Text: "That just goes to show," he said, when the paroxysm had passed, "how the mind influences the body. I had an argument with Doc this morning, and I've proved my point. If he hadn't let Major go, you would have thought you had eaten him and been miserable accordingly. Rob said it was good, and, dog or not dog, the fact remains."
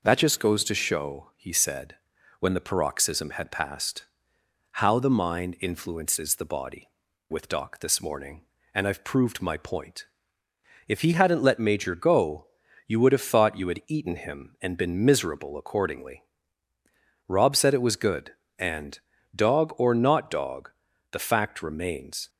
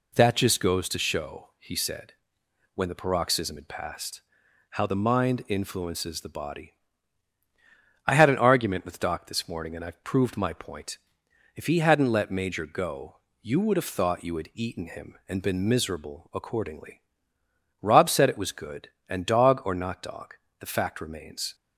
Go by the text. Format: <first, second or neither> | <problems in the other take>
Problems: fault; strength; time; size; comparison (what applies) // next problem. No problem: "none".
second | skips "I had an argument"; at 7.1 s